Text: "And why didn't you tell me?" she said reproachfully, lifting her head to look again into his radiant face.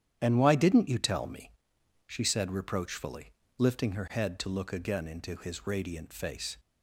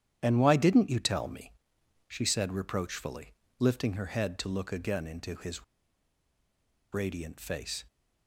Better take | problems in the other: first | starts louder than the rest; strong; until 1.2 s; 10 dB; strong in the first // pauses between "his" and "radiant"; strong; at 5.6 s; 1.3 s long

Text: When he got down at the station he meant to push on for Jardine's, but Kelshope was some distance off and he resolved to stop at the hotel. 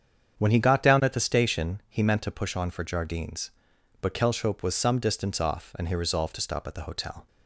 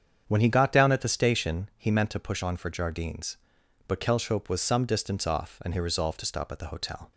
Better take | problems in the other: neither | starts louder than the rest; strong; the same in both

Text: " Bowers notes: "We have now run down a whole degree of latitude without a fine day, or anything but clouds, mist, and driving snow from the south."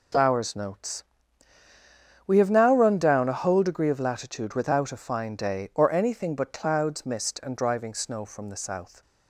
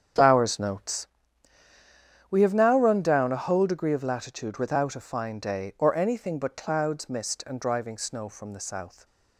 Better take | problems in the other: first | starts louder than the rest; strong; until 1.0 s; 8 dB

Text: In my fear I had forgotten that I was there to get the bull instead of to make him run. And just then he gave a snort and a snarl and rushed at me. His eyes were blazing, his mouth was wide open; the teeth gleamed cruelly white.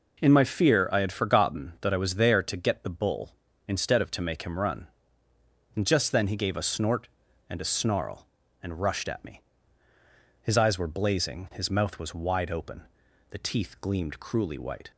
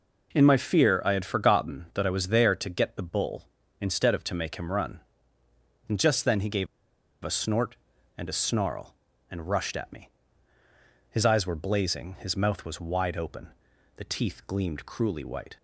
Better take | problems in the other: first | pauses between "gave" and "a"; noticeable; at 6.6 s; 0.57 s long

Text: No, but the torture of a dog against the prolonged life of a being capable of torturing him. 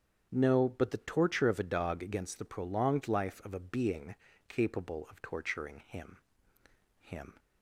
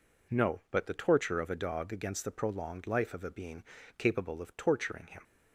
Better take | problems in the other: second | starts louder than the rest; strong; until 1.3 s; 8 dB // pauses between "being" and "capable"; slight; at 4.1 s; 0.34 s long; slight in the second // says "him" twice; at 6.9 s

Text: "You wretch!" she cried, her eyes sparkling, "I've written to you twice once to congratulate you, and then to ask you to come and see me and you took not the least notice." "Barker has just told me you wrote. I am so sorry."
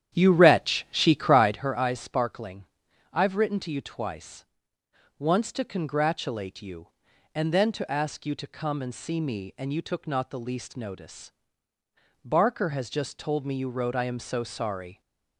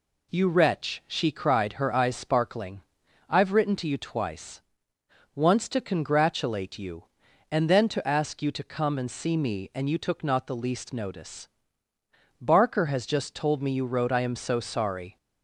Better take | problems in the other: second | starts louder than the rest; strong; until 1.7 s; 10 dB // pauses between "twice" and "once"; noticeable; at 4.4 s; 0.74 s long; noticeable in the second

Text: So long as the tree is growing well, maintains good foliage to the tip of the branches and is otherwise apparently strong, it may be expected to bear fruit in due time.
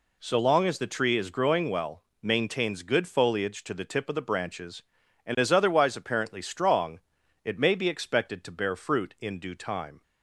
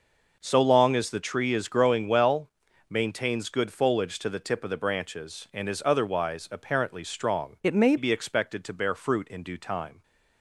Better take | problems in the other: first | changes voice from "it" to "may"; from 7.6 to 7.9 s; 0.3 s long

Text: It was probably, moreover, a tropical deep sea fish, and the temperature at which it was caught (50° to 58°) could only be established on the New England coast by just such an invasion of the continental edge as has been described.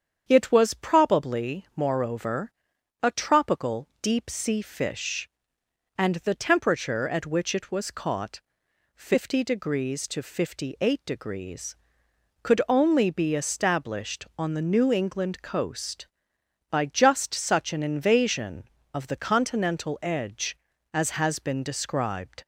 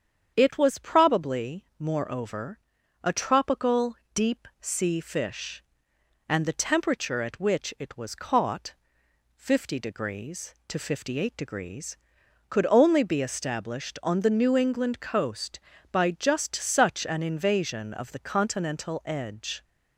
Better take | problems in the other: first | starts louder than the rest; strong; until 1.3 s; 8 dB; strong in the first // pauses between "tropical" and "deep"; slight; at 3.9 s; 0.18 s long // stops before "as has been described"; at 19.6 s

